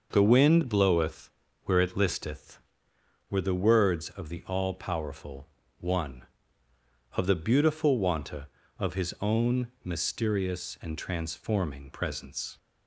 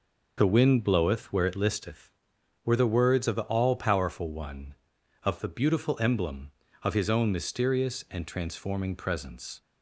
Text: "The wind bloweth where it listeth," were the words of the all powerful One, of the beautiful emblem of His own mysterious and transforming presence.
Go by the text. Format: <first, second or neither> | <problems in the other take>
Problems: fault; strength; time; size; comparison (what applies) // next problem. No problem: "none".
second | starts louder than the rest; noticeable; until 1.1 s; 6 dB // pauses between "bloweth" and "where"; slight; at 1.2 s; 0.34 s long // pauses between "powerful" and "One"; slight; at 5.4 s; 0.32 s long // says "wanta" for "emblem"; at 7.9 s